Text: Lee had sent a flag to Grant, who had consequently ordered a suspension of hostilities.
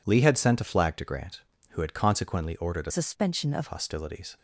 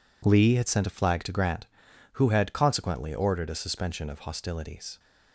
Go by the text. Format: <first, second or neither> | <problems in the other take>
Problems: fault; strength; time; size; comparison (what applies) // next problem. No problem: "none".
second | changes voice from "suspension" to "of"; from 2.9 to 3.6 s; 0.7 s long